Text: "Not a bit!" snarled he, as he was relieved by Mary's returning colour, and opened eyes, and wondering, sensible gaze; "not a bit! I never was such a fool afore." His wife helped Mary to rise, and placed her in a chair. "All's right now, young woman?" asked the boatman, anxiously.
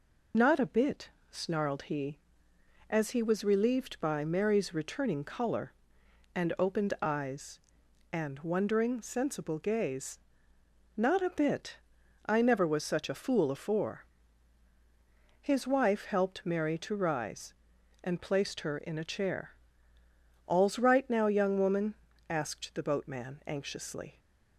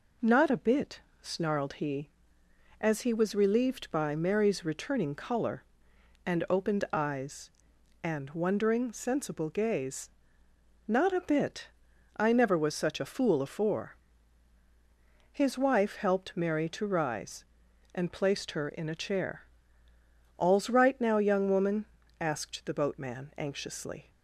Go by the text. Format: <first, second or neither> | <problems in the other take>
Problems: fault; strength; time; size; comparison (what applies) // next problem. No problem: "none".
second | loses the start of "Not"; at 0.3 s; 40 ms